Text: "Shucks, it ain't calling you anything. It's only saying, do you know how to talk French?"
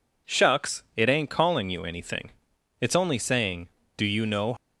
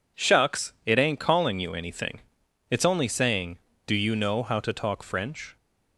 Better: second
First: stops before "how to talk French"; at 4.5 s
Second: none

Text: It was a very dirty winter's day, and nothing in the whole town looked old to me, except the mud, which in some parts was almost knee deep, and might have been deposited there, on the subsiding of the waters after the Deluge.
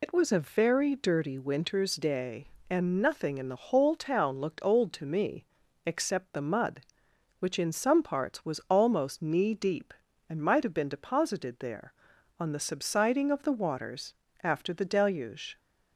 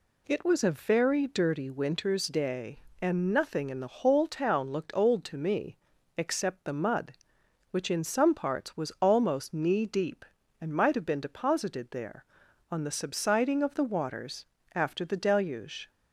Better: second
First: loses the start of "It"; at 0.0 s; 80 ms // pauses between "waters" and "after"; slight; at 14.1 s; 0.28 s long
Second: pauses between "waters" and "after"; slight; at 14.4 s; 0.28 s long

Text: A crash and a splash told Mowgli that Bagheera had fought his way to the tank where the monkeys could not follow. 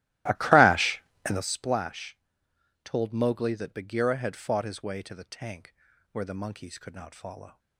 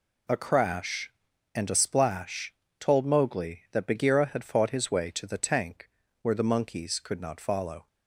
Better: second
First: starts louder than the rest; strong; until 1.5 s; 16.5 dB // pauses between "splash" and "told"; noticeable; at 2.1 s; 0.66 s long // pauses between "tank" and "where"; at 5.7 s; 0.38 s long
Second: pauses between "splash" and "told"; slight; at 2.5 s; 0.28 s long // pauses between "tank" and "where"; slight; at 5.8 s; 0.32 s long

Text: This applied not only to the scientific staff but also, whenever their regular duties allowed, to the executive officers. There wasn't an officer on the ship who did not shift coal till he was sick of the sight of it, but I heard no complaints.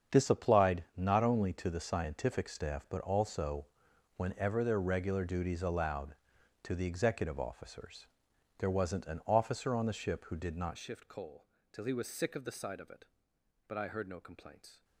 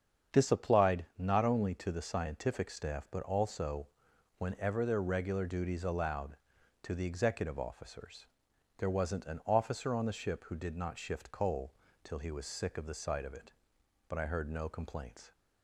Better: second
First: starts louder than the rest; strong; until 1.2 s; 7.5 dB // changes voice at "shift"; from 10.7 s on; 4.1 s long // pauses between "coal" and "till"; slight; at 11.4 s; 0.26 s long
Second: starts louder than the rest; strong; until 1.4 s; 7.5 dB // pauses between "coal" and "till"; slight; at 11.7 s; 0.30 s long

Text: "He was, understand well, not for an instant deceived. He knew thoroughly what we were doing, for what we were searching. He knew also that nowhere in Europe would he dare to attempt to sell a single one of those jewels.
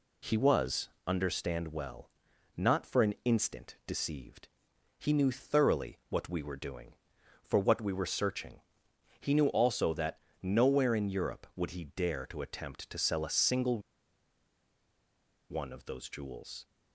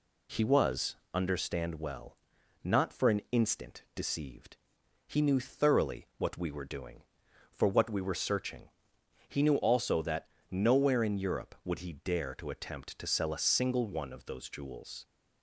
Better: second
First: pauses between "that" and "nowhere"; slight; at 10.2 s; 0.20 s long // pauses between "single" and "one"; strong; at 13.7 s; 1.7 s long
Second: pauses between "that" and "nowhere"; slight; at 10.3 s; 0.20 s long

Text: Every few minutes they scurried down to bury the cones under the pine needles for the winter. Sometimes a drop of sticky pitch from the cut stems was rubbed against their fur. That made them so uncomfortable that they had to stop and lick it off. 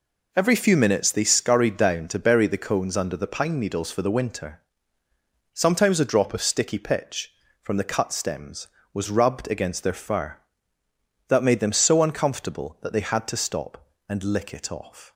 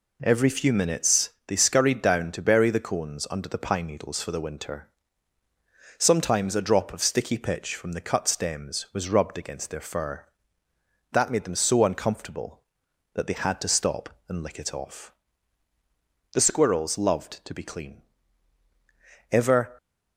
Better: first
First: none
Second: pauses between "minutes" and "they"; slight; at 1.3 s; 0.16 s long // goes on to say "The squirrels loved to be clean Ever"; strong; from 16.3 s on; 3.4 s long

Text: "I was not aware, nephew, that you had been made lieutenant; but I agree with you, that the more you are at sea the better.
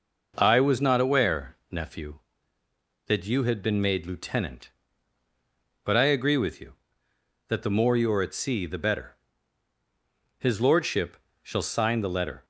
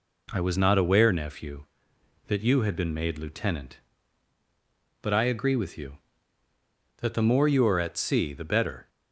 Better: second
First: goes on to say "His lordship shall sign the letter"; strong; from 10.3 s on; 2.0 s long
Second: none

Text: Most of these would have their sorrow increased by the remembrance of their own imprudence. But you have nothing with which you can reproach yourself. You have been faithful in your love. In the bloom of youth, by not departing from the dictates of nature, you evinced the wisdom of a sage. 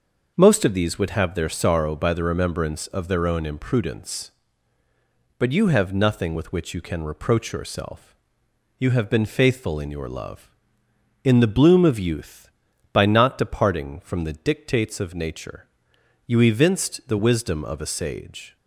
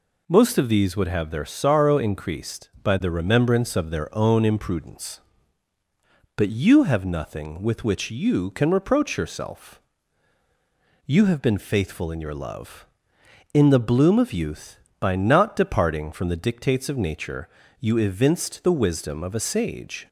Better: second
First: starts louder than the rest; noticeable; until 1.3 s; 6 dB // skips "increased"; at 1.9 s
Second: none

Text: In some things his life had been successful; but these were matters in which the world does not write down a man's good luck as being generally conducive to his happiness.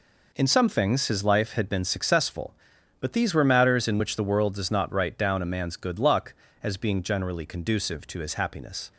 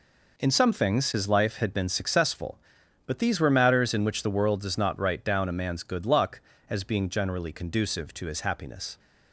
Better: neither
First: none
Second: none

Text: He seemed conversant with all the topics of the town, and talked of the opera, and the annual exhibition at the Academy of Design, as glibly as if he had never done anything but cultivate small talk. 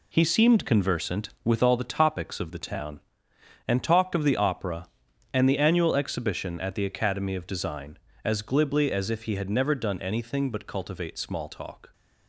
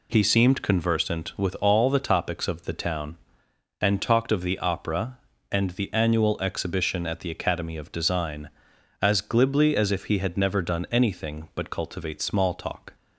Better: second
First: gets quieter; strong; throughout; 8 dB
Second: none

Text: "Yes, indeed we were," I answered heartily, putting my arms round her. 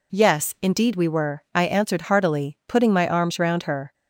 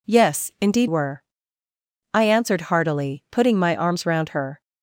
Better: first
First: none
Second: skips "we"; at 0.8 s

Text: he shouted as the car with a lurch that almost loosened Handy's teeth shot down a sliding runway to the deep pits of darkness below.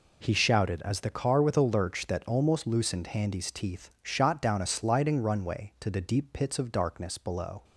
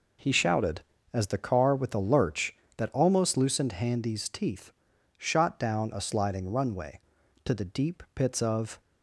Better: first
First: none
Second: pauses between "teeth" and "shot"; noticeable; at 4.6 s; 0.48 s long // stops before "darkness below"; at 8.7 s

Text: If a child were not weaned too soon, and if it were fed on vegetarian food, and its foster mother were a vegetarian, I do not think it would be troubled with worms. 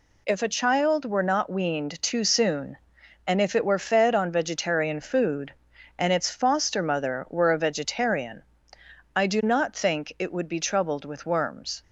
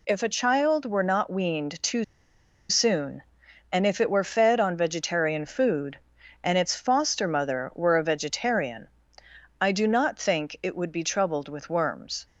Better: first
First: none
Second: pauses between "too" and "soon"; noticeable; at 2.0 s; 0.64 s long

